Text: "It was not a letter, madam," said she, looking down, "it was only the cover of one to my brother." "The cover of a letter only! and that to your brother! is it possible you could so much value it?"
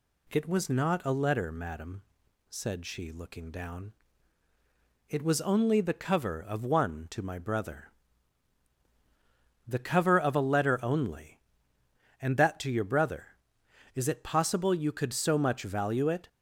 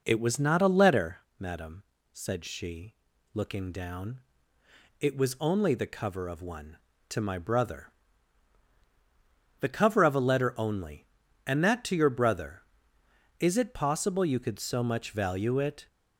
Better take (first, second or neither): first